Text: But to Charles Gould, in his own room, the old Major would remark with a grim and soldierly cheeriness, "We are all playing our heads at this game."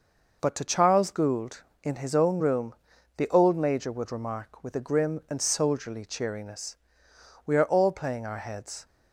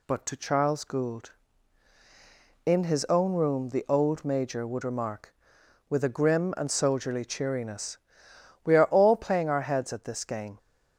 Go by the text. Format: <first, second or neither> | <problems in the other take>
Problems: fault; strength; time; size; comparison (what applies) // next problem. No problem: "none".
second | stops before "at this game"; at 8.8 s